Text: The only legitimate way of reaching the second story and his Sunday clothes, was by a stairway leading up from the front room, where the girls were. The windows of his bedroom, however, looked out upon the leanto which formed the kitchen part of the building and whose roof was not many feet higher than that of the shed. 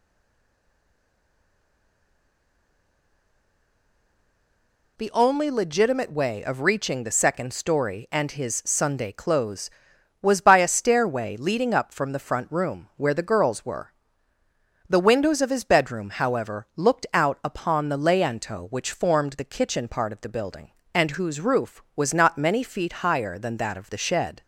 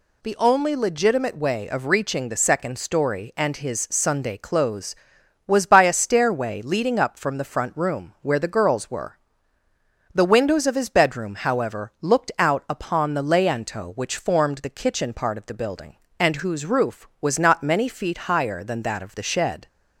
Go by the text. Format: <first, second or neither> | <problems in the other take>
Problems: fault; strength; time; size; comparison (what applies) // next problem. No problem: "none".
second | stays silent before the first word; strong; until 4.9 s; 4.9 s long